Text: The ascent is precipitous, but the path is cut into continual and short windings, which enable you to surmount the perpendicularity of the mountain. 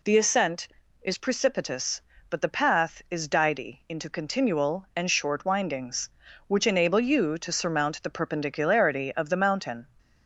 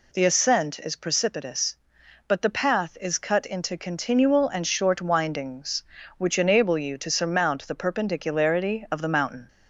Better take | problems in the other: second | says "didy" for "cut"; at 3.2 s

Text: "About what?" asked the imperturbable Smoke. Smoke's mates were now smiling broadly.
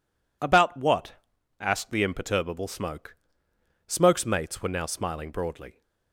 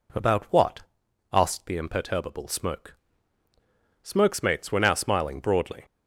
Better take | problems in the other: neither | none

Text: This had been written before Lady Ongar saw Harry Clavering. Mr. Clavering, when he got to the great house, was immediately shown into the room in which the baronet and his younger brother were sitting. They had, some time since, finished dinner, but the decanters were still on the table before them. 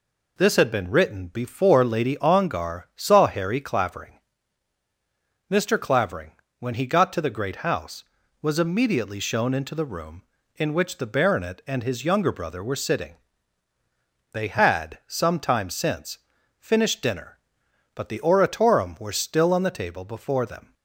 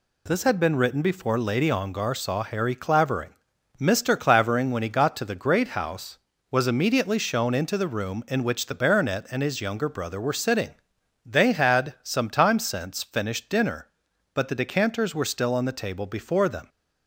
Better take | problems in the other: second | says "oratorum" for "decanters"; at 18.1 s

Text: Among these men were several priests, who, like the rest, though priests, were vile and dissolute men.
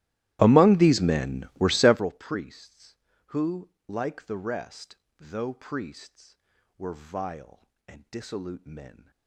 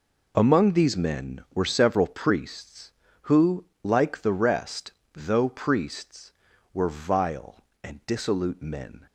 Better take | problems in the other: second | starts louder than the rest; strong; until 2.0 s; 15.5 dB

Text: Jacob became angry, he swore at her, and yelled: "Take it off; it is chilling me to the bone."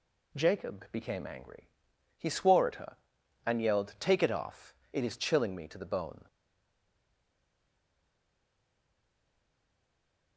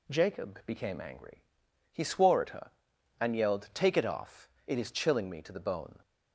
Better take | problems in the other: second | stays silent after the last word; strong; from 6.2 s on; 4.1 s long

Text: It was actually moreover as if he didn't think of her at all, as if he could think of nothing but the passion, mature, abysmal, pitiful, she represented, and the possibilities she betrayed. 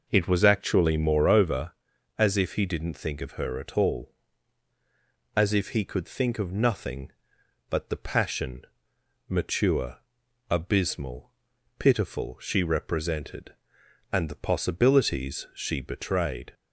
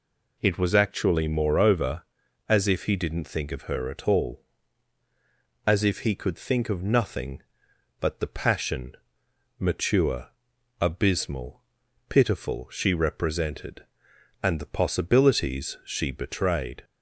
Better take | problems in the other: second | starts louder than the rest; noticeable; until 1.6 s; 5 dB

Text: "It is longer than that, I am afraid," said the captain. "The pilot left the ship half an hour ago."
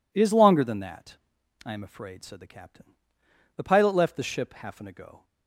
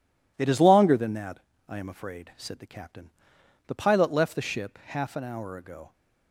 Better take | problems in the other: second | skips "hour"; at 4.8 s

